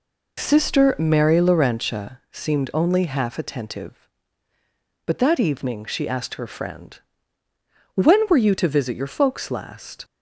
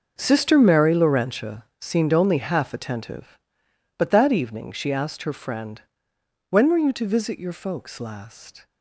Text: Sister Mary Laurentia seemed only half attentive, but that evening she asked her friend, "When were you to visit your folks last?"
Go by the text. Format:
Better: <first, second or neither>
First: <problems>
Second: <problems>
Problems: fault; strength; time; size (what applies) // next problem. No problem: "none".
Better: first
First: none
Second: gets quieter; strong; throughout; 14 dB // pauses between "Laurentia" and "seemed"; slight; at 1.6 s; 0.16 s long